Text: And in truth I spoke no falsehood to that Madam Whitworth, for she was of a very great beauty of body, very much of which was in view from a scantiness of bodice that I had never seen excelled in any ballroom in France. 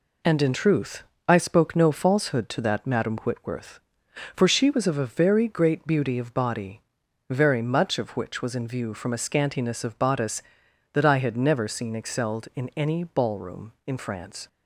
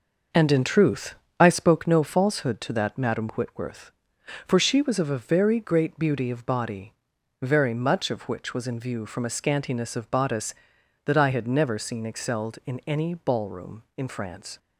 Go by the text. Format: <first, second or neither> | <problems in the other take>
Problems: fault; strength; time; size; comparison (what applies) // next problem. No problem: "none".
first | starts louder than the rest; noticeable; until 1.8 s; 6 dB // pauses between "truth" and "I"; slight; at 1.1 s; 0.24 s long; slight in the first